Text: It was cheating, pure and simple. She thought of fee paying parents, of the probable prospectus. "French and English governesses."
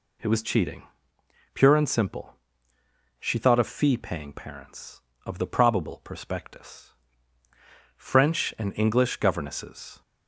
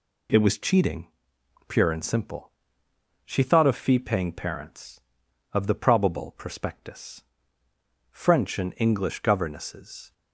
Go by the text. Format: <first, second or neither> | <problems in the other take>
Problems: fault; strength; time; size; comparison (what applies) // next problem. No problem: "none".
neither | none